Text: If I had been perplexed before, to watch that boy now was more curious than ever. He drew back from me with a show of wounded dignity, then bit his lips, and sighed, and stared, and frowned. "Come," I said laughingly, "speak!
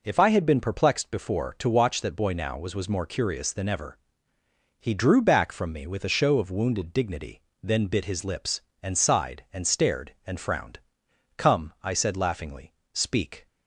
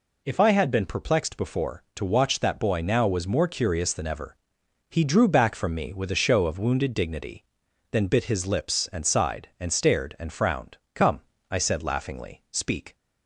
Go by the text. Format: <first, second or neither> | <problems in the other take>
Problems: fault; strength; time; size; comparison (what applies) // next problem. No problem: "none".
second | says "was" twice; at 2.7 s